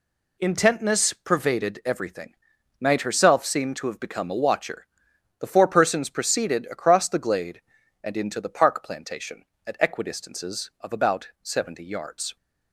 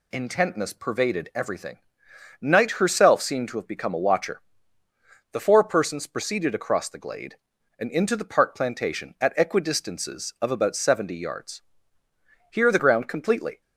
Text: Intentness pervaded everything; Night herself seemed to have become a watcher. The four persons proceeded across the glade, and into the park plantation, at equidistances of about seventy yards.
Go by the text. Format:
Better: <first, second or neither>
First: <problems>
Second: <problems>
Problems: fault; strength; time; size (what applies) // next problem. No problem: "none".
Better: first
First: none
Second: goes on to say "Here the ground completely"; noticeable; from 12.5 s on; 1.1 s long